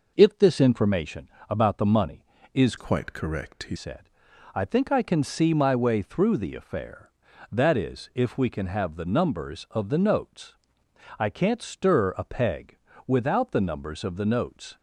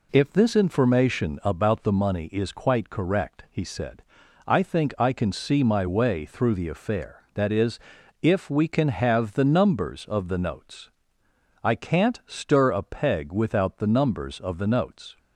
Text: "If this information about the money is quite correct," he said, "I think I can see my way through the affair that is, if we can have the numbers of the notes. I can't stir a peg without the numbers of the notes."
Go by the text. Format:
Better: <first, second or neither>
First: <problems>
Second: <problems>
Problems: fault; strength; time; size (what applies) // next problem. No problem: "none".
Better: second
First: pauses between "information" and "about"; slight; at 1.2 s; 0.20 s long // changes voice from "quite" to "he"; from 2.7 to 3.7 s; 1.0 s long // pauses between "peg" and "without"; slight; at 12.7 s; 0.30 s long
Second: none